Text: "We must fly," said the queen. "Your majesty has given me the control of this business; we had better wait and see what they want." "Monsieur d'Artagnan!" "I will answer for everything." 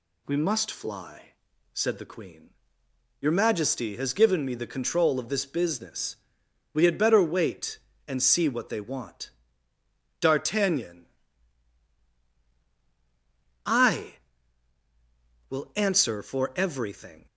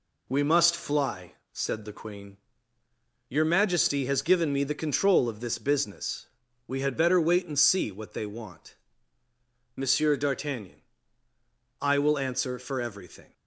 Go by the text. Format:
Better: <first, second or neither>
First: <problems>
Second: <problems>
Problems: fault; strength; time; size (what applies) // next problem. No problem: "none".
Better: second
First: skips "Monsieur"; at 9.7 s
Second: none